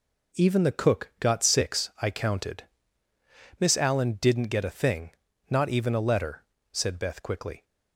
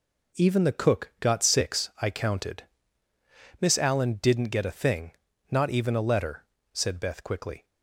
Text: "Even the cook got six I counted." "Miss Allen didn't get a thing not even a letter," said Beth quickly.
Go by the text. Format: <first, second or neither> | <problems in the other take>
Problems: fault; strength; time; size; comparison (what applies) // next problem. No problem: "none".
neither | pauses between "thing" and "not"; the same in both